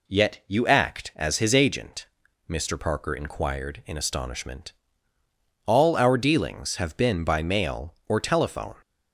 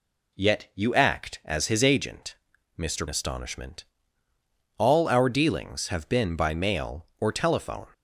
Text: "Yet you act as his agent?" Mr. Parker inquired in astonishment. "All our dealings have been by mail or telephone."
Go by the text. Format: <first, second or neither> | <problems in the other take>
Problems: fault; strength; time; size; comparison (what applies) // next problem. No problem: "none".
first | skips "Parker inquired in"; at 3.0 s